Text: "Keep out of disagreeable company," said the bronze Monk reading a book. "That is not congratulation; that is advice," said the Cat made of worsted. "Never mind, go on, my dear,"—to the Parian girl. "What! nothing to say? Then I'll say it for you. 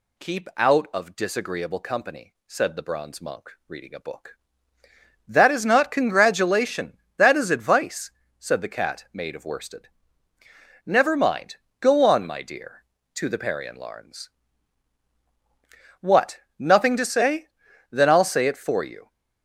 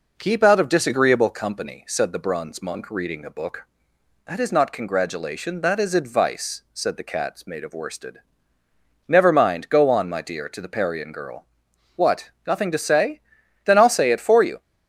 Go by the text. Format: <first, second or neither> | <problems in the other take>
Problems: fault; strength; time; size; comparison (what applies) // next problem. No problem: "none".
second | says "larns" for "girl"; at 13.7 s